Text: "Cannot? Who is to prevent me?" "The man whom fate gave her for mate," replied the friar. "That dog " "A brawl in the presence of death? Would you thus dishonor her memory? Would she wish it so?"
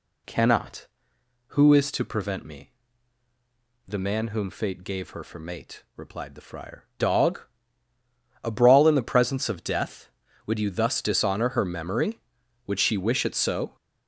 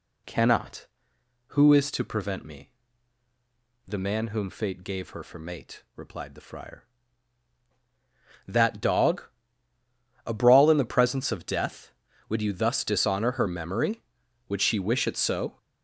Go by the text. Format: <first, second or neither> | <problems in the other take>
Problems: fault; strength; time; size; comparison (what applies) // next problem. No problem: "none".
second | skips "That"; at 6.9 s